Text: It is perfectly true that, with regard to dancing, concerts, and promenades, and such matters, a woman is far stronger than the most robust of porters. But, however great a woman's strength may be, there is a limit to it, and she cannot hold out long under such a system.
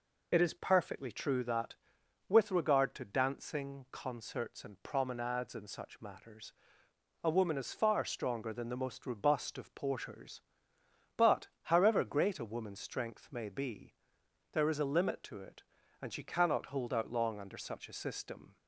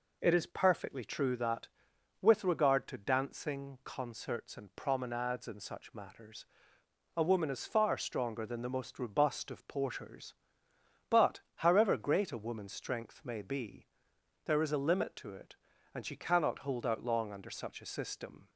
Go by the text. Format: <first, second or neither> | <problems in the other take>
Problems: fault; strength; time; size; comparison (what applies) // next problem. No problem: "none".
second | loses the start of "It"; at 0.3 s; 40 ms